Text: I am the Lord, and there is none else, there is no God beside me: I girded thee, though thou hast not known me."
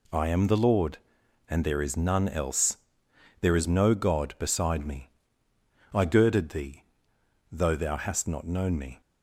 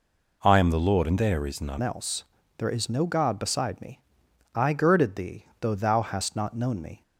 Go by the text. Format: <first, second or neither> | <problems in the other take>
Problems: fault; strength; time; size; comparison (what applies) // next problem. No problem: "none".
first | changes voice at "else"; from 1.8 s on; 5.2 s long